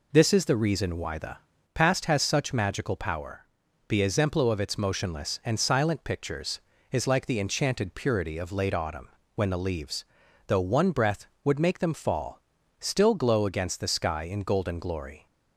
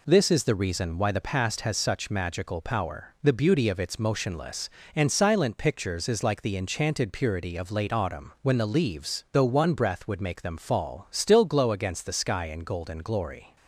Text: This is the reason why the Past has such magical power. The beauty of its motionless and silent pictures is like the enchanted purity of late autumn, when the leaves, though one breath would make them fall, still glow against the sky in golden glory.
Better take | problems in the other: second | pauses between "the" and "Past"; at 1.3 s; 0.38 s long // says "exemplo" for "beauty"; at 4.0 s

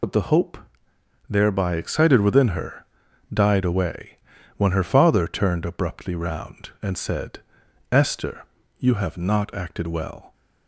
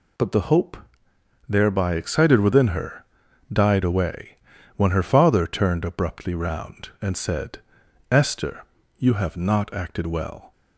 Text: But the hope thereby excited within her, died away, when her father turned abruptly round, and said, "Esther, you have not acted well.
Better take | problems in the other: second | loses the start of "But"; at 0.0 s; 45 ms // pauses between "hope" and "thereby"; noticeable; at 0.5 s; 0.72 s long; noticeable in the second

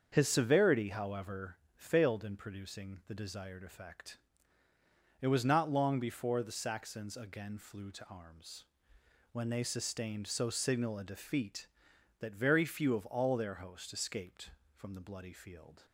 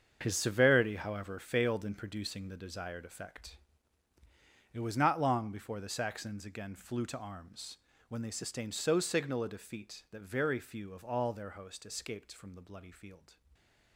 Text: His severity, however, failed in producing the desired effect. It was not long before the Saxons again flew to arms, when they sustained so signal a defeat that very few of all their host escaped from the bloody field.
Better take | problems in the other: first | gets quieter; strong; throughout; 11 dB // starts louder than the rest; until 1.2 s; 7 dB; also in the first

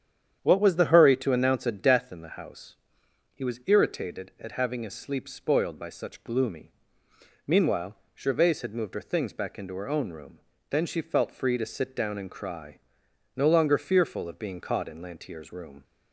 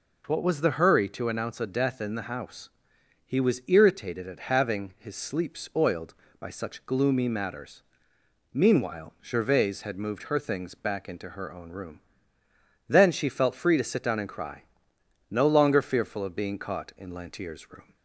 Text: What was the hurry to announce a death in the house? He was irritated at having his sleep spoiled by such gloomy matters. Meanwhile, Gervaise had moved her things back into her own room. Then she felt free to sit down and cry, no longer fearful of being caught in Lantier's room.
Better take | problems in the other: second | starts louder than the rest; strong; until 1.4 s; 8.5 dB // skips "matters"; at 7.0 s

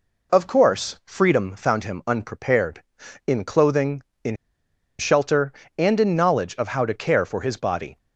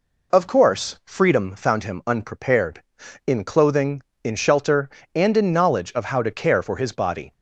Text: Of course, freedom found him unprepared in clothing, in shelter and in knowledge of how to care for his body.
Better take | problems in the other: second | pauses between "in" and "shelter"; noticeable; at 4.3 s; 0.63 s long

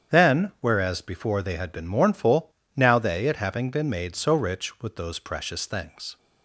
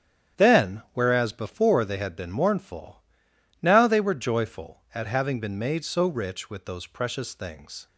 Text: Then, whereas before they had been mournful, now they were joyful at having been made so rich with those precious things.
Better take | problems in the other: second | starts louder than the rest; strong; until 1.2 s; 8.5 dB; strong in the second // skips "were joyful"; at 3.2 s

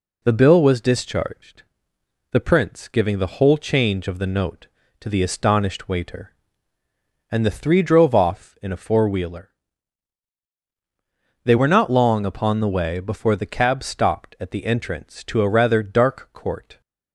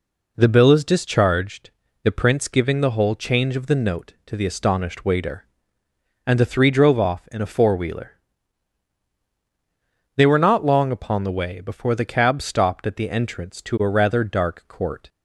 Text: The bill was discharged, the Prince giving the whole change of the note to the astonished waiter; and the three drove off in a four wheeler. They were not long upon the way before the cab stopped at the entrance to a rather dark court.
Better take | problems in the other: first | says "is" for "was"; at 0.7 s

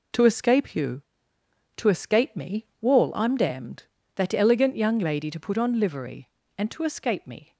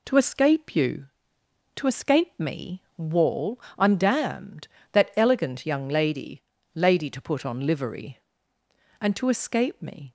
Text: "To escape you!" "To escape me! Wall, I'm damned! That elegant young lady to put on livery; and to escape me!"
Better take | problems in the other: first | says "lady" twice; at 6.7 s

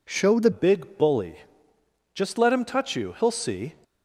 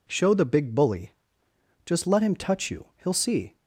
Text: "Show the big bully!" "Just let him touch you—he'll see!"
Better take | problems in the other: second | changes voice at "big"; from 0.5 s on; 3.2 s long

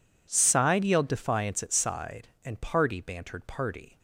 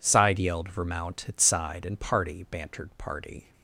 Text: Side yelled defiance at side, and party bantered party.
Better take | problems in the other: first | says "vermount" for "defiance"; at 0.7 s

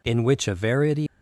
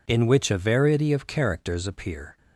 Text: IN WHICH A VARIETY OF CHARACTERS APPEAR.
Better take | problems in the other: second | stops before "OF CHARACTERS APPEAR"; at 1.0 s

